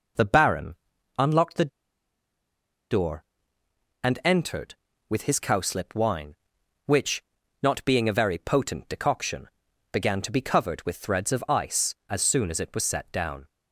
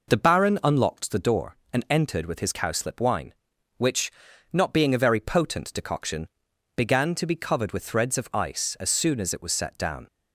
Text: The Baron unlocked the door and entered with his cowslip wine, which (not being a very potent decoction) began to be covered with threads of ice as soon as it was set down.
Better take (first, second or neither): second